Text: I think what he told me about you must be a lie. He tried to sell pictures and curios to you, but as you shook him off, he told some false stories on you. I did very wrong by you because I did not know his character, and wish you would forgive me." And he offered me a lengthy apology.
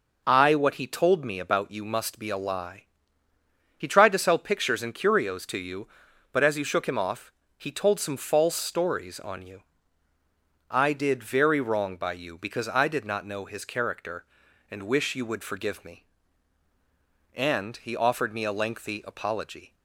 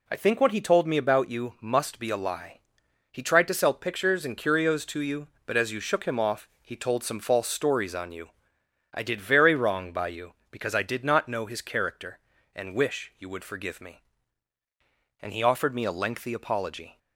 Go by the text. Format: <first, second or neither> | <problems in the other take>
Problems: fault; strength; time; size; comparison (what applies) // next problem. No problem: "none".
second | skips "think"; at 0.5 s